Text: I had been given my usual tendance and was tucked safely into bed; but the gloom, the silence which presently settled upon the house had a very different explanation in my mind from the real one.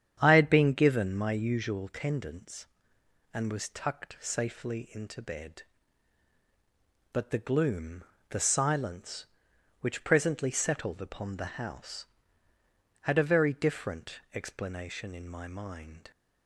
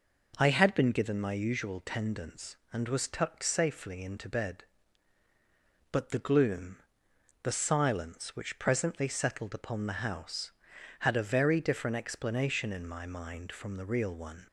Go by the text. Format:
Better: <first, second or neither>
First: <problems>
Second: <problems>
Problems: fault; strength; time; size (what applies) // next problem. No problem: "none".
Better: second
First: starts louder than the rest; strong; until 1.2 s; 9 dB // stops before "from the real one"; at 16.1 s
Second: none